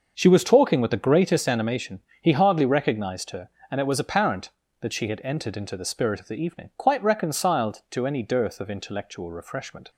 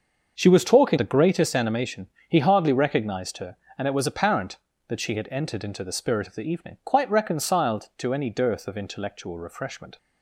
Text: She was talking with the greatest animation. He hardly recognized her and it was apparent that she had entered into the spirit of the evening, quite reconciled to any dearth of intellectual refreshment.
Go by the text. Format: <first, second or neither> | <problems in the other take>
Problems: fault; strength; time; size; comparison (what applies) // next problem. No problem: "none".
first | starts louder than the rest; until 1.3 s; 6.5 dB; also in the first // skips "with"; at 0.9 s